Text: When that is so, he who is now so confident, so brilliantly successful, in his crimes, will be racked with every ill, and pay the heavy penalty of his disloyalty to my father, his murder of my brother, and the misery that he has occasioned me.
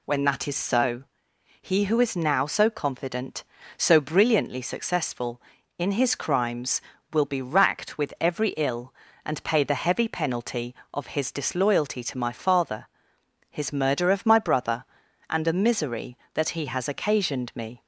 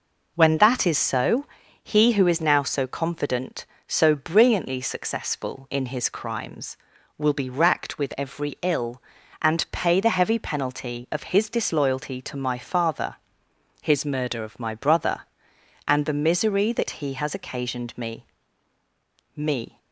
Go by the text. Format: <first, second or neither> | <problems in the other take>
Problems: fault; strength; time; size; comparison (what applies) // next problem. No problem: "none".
first | says "me" twice; at 19.3 s